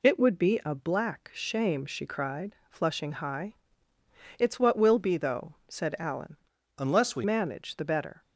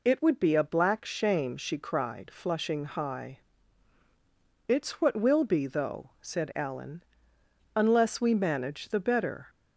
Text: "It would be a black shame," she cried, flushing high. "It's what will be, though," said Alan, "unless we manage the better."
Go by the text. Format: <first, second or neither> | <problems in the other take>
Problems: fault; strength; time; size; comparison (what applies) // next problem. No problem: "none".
second | changes voice from "unless" to "we"; from 6.7 to 7.2 s; 0.5 s long